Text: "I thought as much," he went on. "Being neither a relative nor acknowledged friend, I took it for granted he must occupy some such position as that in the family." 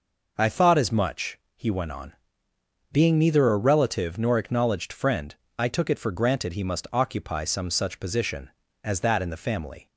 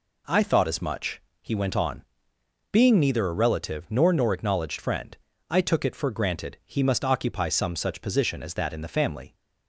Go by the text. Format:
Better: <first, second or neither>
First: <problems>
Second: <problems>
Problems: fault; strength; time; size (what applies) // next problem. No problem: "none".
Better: first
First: none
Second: says "nor" twice; at 4.1 s